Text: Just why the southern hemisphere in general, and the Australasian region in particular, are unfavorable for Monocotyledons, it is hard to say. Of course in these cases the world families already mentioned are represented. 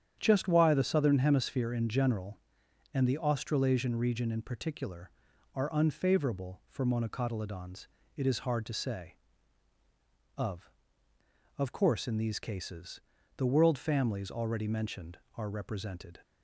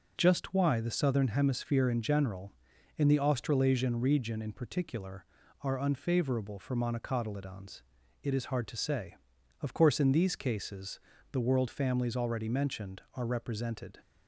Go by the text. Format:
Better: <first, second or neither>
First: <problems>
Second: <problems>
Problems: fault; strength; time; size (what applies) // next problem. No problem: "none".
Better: second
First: starts louder than the rest; strong; until 1.2 s; 9 dB // says "Of" twice; at 11.5 s // pauses between "cases" and "the"; slight; at 13.0 s; 0.36 s long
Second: pauses between "cases" and "the"; slight; at 10.9 s; 0.34 s long